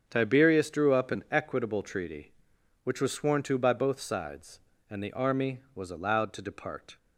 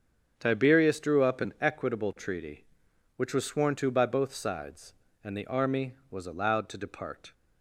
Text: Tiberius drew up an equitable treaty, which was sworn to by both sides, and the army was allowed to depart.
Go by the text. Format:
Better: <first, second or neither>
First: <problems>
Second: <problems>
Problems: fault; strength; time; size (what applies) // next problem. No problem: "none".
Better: neither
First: starts louder than the rest; strong; until 1.0 s; 7.5 dB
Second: starts louder than the rest; strong; until 1.3 s; 7.5 dB